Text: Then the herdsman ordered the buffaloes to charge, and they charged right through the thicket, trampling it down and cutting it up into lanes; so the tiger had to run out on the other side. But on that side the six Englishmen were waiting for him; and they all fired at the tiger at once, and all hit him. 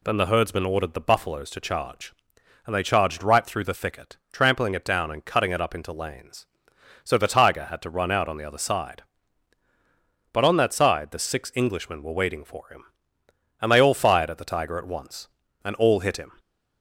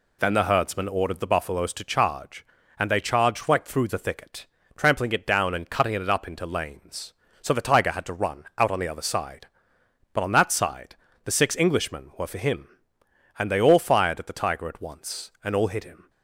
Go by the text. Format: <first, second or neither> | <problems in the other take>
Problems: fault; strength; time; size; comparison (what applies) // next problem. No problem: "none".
first | pauses between "side" and "the"; slight; at 10.9 s; 0.28 s long // skips "waiting"; at 12.2 s